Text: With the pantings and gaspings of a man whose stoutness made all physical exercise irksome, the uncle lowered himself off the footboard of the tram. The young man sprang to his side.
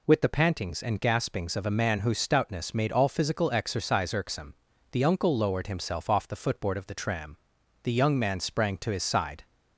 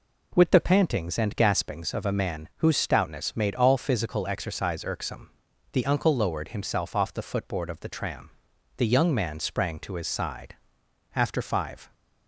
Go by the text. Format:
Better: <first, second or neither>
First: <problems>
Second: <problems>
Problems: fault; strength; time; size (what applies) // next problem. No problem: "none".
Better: first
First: none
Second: goes on to say "After five"; noticeable; from 11.1 s on; 0.78 s long